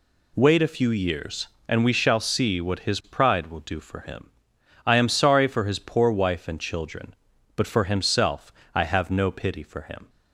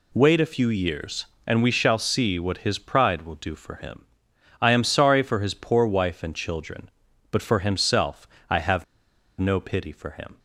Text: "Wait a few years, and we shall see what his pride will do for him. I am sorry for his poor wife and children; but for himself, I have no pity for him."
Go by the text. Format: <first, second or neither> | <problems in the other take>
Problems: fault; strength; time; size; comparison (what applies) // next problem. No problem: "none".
first | pauses between "have" and "no"; noticeable; at 8.8 s; 0.54 s long